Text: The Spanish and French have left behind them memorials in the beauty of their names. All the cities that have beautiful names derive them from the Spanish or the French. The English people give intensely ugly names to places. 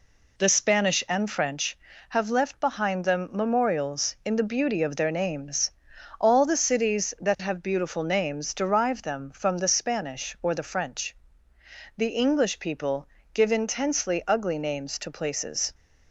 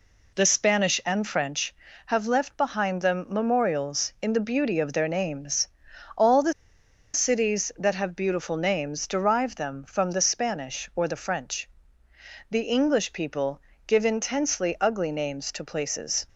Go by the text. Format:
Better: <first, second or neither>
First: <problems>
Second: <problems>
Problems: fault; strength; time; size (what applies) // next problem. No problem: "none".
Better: first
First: pauses between "people" and "give"; slight; at 13.0 s; 0.28 s long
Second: pauses between "the" and "cities"; noticeable; at 6.5 s; 0.62 s long // pauses between "people" and "give"; slight; at 13.5 s; 0.28 s long